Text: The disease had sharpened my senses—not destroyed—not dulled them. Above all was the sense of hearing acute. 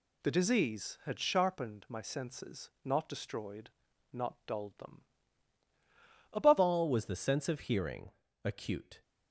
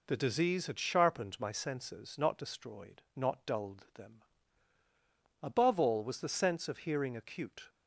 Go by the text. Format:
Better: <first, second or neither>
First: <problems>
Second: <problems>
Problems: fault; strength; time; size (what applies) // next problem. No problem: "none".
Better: second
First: changes voice at "all"; from 6.5 s on; 2.5 s long // pauses between "hearing" and "acute"; slight; at 8.1 s; 0.34 s long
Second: none